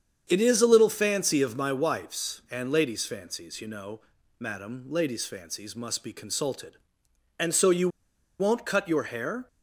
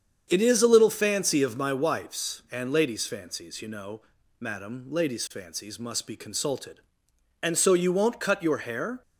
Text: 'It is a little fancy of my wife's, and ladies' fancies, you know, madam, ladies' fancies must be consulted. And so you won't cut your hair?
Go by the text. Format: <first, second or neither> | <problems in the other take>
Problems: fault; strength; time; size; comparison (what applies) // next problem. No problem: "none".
second | starts louder than the rest; strong; until 1.3 s; 8 dB; strong in the second // pauses between "you" and "won't"; noticeable; at 7.8 s; 0.51 s long